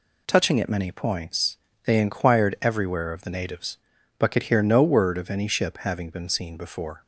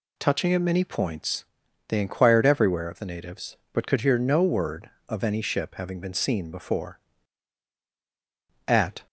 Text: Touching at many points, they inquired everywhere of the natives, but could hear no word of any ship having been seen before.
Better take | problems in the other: first | goes on to say "At"; slight; from 8.6 s on; 0.40 s long

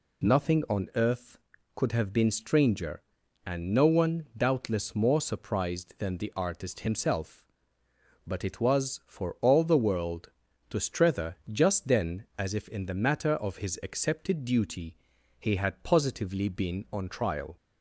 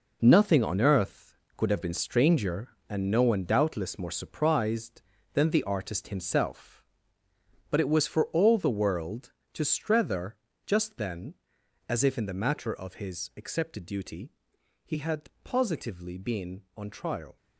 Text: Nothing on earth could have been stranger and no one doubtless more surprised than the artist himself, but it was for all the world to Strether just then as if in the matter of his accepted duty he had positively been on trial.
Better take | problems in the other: first | gets quieter; strong; throughout; 8.5 dB // pauses between "Strether" and "just"; slight; at 10.3 s; 0.28 s long; slight in the first // pauses between "duty" and "he"; noticeable; at 14.3 s; 0.54 s long; noticeable in the first // pauses between "had" and "positively"; slight; at 15.2 s; 0.16 s long

